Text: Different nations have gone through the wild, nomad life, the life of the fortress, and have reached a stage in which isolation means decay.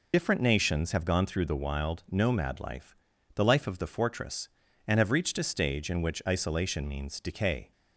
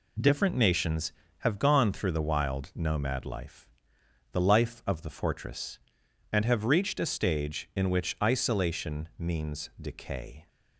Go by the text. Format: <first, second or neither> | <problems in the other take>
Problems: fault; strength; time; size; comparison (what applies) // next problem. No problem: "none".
second | loses the start of "Different"; at 0.1 s; 65 ms